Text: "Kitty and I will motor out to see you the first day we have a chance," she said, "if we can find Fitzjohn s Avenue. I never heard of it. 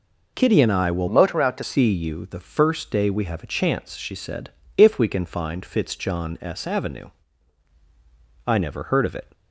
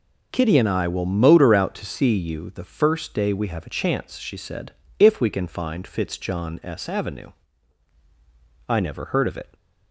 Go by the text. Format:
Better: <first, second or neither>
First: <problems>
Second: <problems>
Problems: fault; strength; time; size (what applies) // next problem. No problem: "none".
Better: second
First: changes voice from "motor" to "to"; from 1.0 to 1.6 s; 0.6 s long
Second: none